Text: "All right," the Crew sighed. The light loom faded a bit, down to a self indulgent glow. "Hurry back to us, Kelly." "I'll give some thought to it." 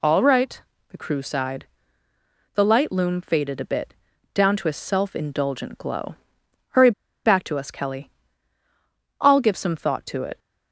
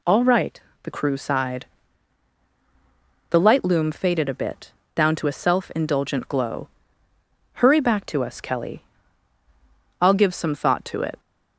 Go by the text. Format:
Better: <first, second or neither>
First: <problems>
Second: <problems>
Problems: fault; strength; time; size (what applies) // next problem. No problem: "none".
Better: second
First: pauses between "Hurry" and "back"; slight; at 6.9 s; 0.34 s long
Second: none